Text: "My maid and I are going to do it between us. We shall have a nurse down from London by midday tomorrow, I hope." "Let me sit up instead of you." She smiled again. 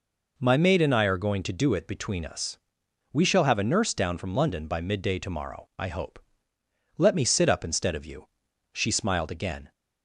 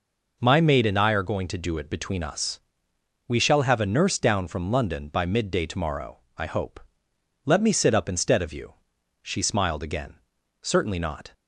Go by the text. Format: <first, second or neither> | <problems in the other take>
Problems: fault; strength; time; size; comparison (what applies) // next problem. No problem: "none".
first | goes on to say "Certainly not"; noticeable; from 10.6 s on; 0.70 s long